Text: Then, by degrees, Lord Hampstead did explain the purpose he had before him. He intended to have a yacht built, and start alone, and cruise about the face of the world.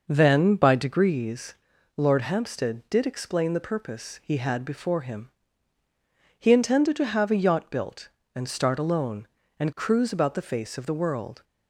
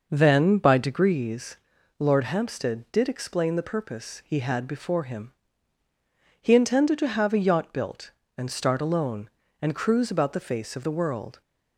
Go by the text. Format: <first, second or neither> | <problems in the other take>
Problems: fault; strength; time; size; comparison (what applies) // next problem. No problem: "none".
neither | none